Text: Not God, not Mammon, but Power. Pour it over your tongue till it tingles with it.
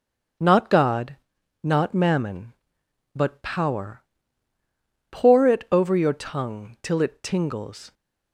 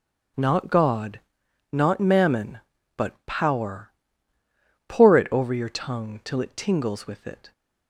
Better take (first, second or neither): second